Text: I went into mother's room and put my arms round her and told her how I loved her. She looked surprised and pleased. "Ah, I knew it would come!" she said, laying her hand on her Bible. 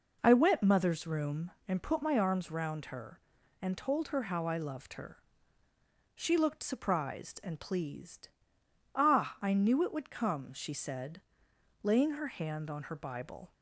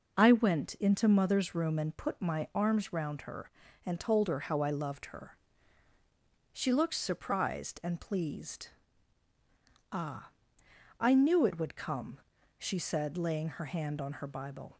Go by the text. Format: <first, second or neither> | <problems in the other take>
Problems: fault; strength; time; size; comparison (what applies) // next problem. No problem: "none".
second | skips "into"; at 0.6 s